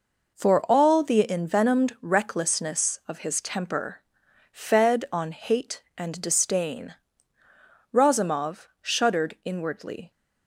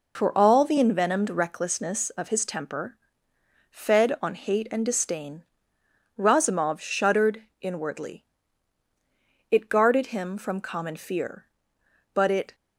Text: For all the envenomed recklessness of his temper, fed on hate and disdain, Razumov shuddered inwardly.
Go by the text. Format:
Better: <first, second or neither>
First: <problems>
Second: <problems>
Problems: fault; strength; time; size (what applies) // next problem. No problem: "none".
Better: first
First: none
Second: pauses between "shuddered" and "inwardly"; slight; at 7.4 s; 0.18 s long // goes on to say "It guarded him from common fear but it"; strong; from 9.5 s on; 3.0 s long